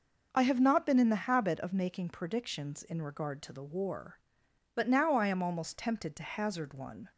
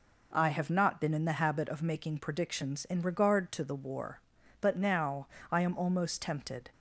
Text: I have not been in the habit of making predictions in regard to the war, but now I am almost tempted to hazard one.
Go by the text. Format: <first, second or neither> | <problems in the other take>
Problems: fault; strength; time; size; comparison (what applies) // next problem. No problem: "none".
first | pauses between "now" and "I"; slight; at 5.2 s; 0.24 s long // stops before "to hazard one"; at 6.7 s